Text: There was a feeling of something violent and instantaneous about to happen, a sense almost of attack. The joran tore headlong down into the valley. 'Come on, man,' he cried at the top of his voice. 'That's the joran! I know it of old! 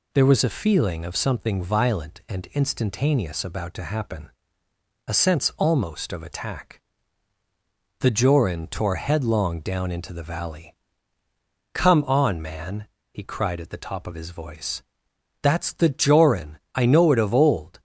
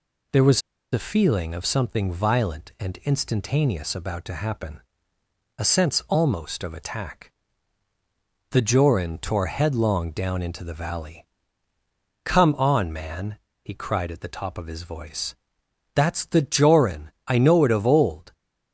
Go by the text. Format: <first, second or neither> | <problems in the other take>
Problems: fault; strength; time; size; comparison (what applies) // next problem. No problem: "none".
first | pauses between "was" and "a"; slight; at 0.6 s; 0.31 s long